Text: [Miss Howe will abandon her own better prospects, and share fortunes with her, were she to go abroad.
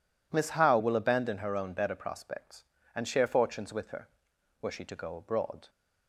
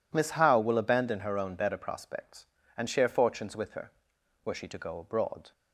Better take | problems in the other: neither | none

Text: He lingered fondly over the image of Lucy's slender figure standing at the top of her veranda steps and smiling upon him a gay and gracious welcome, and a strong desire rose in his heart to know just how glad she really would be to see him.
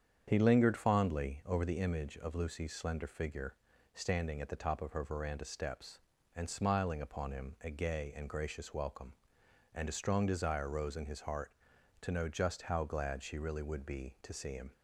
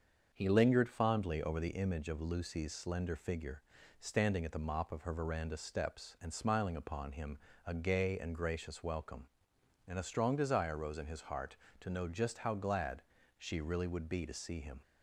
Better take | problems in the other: first | starts louder than the rest; until 1.3 s; 6.5 dB; strong in the first // pauses between "figure" and "standing"; at 3.6 s; 0.40 s long; also in the first // says "mop" for "top"; at 4.5 s // pauses between "him" and "a"; slight; at 7.3 s; 0.30 s long // pauses between "glad" and "she"; slight; at 13.0 s; 0.36 s long

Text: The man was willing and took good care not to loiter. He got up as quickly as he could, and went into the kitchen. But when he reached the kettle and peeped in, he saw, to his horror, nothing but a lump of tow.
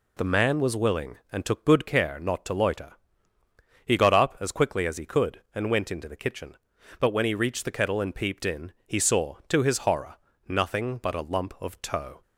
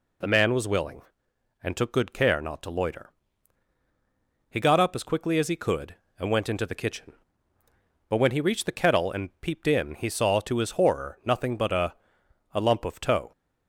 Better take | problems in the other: first | says "a" twice; at 12.5 s

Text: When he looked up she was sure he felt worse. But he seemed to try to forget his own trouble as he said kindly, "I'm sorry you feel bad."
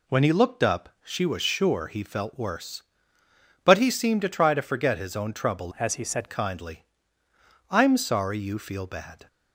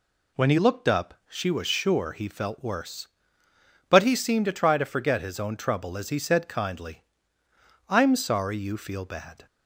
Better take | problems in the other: second | changes voice from "as" to "said"; from 5.7 to 6.2 s; 0.5 s long

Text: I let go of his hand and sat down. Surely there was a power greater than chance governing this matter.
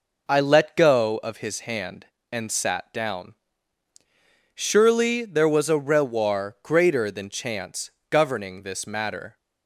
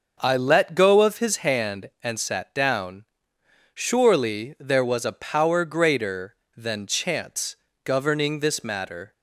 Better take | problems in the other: second | says "rewar" for "power"; at 5.7 s // pauses between "chance" and "governing"; slight; at 7.9 s; 0.20 s long; slight in the second

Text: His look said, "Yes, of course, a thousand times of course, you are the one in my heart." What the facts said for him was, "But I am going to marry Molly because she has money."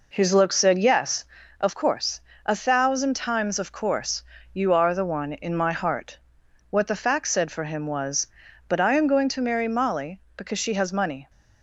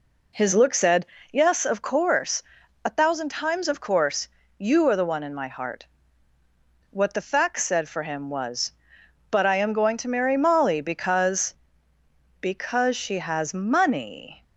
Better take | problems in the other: first | says "because" twice; at 12.4 s

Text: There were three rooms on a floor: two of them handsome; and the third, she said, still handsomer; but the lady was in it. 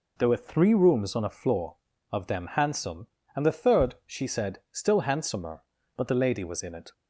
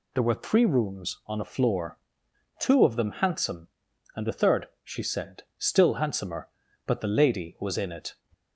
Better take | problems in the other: second | skips "two"; at 1.9 s

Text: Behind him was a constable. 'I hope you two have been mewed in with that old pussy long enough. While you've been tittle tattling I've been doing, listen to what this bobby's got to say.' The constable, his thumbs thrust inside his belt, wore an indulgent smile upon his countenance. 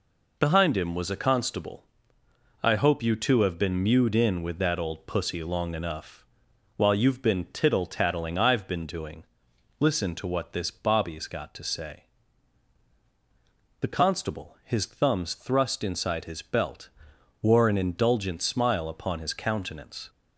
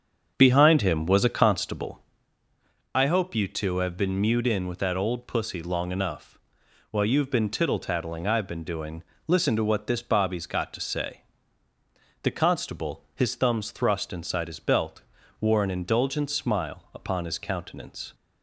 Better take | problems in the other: first | starts louder than the rest; strong; until 1.9 s; 7.5 dB

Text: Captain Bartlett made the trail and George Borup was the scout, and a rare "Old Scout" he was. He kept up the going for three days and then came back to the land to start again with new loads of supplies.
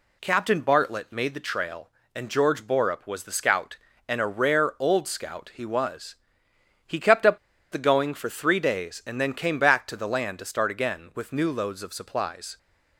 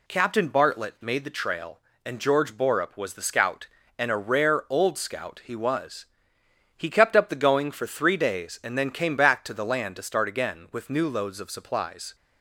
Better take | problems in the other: second | pauses between "up" and "the"; slight; at 7.3 s; 0.33 s long

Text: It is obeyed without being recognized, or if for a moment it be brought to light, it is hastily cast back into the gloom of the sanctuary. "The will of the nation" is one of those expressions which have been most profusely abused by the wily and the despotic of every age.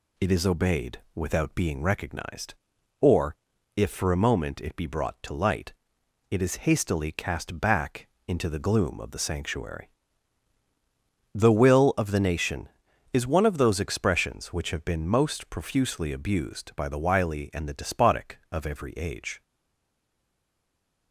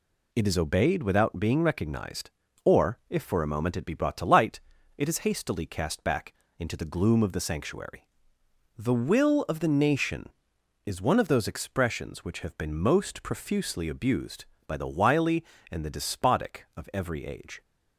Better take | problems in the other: second | pauses between "obeyed" and "without"; slight; at 0.9 s; 0.16 s long // pauses between "or" and "if"; at 3.3 s; 0.40 s long // pauses between "back" and "into"; slight; at 8.0 s; 0.20 s long; slight in the second // stays silent after the last word; noticeable; from 19.4 s on; 1.7 s long

